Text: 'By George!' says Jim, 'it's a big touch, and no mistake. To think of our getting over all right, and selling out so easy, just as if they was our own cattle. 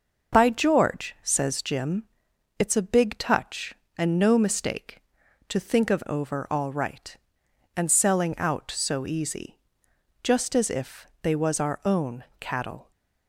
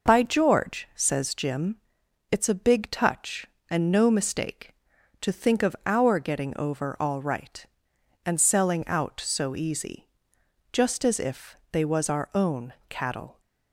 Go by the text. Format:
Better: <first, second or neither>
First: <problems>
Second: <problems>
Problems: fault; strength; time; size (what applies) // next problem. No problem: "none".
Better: second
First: skips "our getting"; at 6.0 s // pauses between "if" and "they"; slight; at 11.0 s; 0.16 s long // pauses between "own" and "cattle"; slight; at 12.2 s; 0.16 s long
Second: pauses between "if" and "they"; slight; at 11.5 s; 0.16 s long // pauses between "own" and "cattle"; slight; at 12.7 s; 0.16 s long